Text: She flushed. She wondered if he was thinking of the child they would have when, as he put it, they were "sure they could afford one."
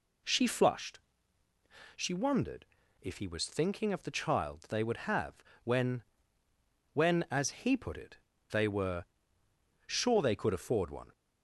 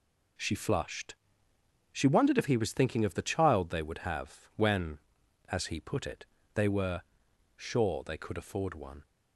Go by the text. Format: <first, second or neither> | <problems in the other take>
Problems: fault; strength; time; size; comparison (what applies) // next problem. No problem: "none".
second | pauses between "wondered" and "if"; at 2.6 s; 0.38 s long // pauses between "have" and "when"; slight; at 5.3 s; 0.28 s long // says "when" twice; at 6.9 s // pauses between "were" and "sure"; noticeable; at 9.0 s; 0.82 s long; noticeable in the second